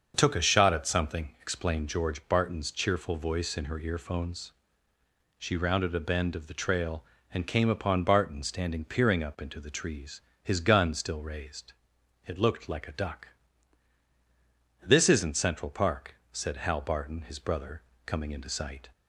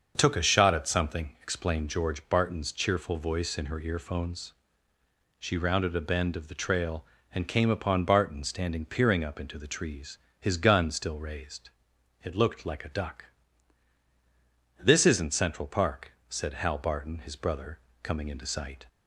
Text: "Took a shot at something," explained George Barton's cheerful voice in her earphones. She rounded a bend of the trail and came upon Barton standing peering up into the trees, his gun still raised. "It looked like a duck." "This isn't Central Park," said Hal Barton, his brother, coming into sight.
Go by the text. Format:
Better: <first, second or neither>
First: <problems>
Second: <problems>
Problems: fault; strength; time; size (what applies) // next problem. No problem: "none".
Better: neither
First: starts louder than the rest; until 1.1 s; 7 dB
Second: starts louder than the rest; until 1.1 s; 7 dB